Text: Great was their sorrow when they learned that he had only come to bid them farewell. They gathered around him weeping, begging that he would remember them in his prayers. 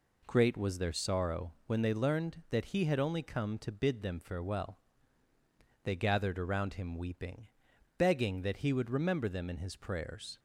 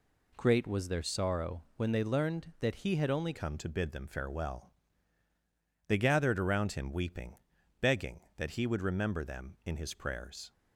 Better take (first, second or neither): first